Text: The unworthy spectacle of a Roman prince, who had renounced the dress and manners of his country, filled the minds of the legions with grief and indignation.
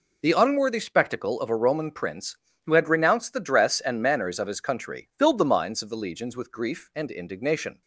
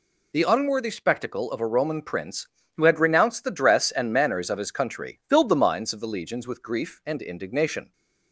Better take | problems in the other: second | starts louder than the rest; noticeable; until 1.8 s; 4 dB

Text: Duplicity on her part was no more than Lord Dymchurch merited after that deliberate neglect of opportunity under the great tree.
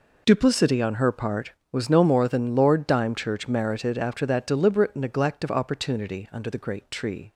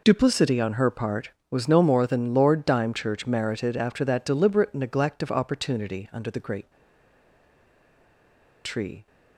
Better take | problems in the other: first | pauses between "great" and "tree"; strong; at 6.7 s; 1.9 s long

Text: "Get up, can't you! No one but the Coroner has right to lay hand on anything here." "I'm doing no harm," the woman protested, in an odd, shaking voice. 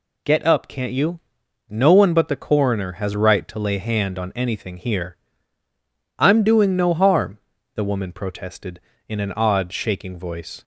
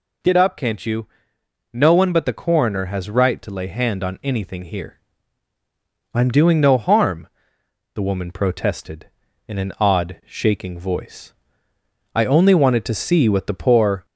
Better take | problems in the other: first | goes on to say "I only wanted to see what the poor"; strong; from 12.1 s on; 1.9 s long

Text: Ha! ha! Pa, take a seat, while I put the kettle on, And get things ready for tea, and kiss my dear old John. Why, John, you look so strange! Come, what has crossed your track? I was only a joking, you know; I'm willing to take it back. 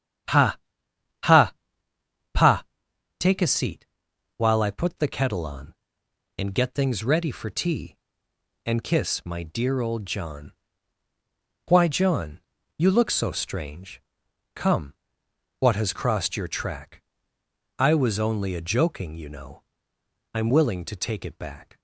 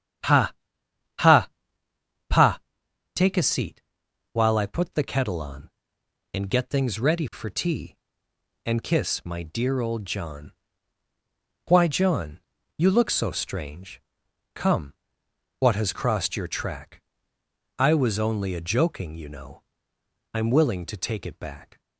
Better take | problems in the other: neither | starts louder than the rest; strong; the same in both

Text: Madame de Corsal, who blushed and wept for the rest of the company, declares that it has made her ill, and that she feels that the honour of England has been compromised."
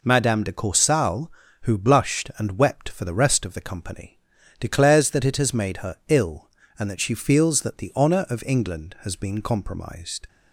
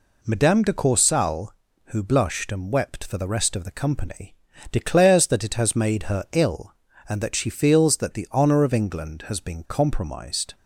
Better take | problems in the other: neither | none

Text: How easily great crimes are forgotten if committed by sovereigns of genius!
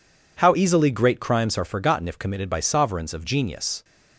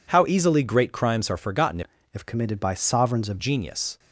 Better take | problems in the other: first | changes voice from "if" to "of"; from 2.1 to 3.3 s; 1.2 s long

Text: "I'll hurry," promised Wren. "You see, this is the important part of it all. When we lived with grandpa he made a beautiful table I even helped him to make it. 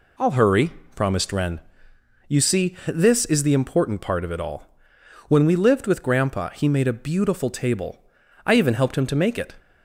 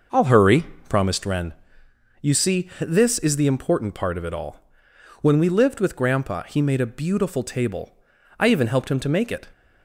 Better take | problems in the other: first | starts louder than the rest; noticeable; until 1.1 s; 6 dB // pauses between "table" and "I"; at 7.9 s; 0.42 s long; also in the first

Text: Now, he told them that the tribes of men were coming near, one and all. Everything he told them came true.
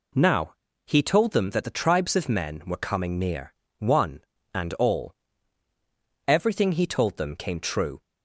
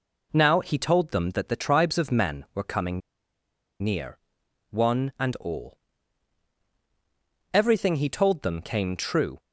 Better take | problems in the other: first | pauses between "coming" and "near"; noticeable; at 3.0 s; 0.82 s long

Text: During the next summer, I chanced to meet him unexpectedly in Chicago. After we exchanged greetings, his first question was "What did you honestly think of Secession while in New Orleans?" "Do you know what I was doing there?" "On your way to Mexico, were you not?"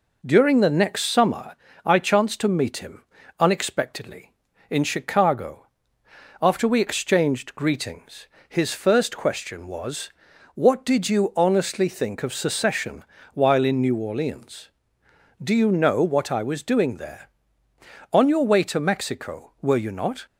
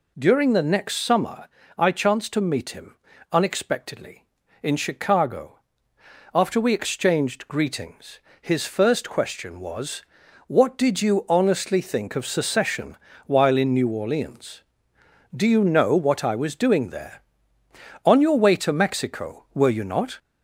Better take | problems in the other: first | gets louder; slight; throughout; 3 dB // pauses between "him" and "unexpectedly"; slight; at 2.9 s; 0.36 s long; slight in the first // pauses between "was" and "What"; noticeable; at 10.0 s; 0.46 s long; noticeable in the first // pauses between "Secession" and "while"; slight; at 12.9 s; 0.28 s long; slight in the first

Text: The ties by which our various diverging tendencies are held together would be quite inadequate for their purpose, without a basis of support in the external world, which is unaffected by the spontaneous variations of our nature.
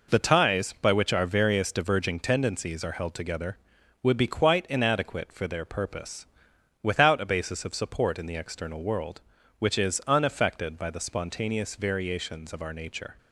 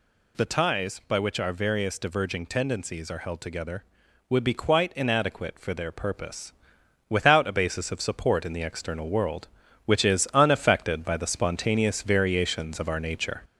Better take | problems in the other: first | gets louder; slight; throughout; 3 dB

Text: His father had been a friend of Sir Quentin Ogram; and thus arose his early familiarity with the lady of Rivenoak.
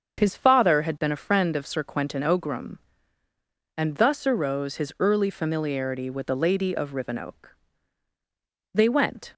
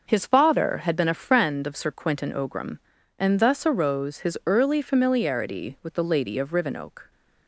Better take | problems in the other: second | starts louder than the rest; until 1.2 s; 7 dB; also in the second // goes on to say "They went"; noticeable; from 8.7 s on; 0.62 s long

